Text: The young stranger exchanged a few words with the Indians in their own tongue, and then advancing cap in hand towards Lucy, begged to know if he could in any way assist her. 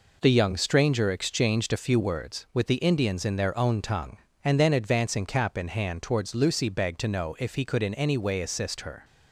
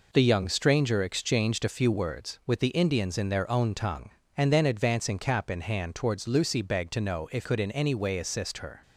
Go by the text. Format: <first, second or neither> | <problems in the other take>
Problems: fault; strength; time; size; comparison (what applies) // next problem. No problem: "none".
first | skips "he"; at 7.4 s